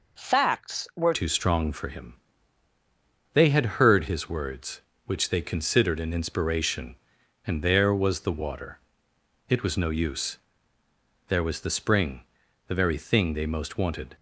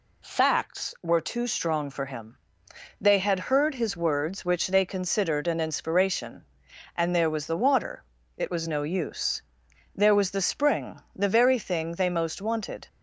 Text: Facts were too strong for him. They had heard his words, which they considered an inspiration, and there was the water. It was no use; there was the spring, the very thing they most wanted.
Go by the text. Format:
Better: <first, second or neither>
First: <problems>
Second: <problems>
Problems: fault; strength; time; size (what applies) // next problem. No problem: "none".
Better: second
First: changes voice at "too"; from 1.1 s on; 13.0 s long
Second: none